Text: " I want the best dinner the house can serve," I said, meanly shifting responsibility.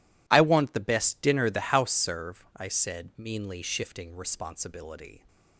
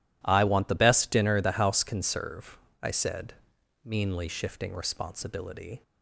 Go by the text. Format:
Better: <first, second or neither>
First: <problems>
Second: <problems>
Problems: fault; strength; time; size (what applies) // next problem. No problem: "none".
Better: second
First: skips "can"; at 1.9 s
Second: none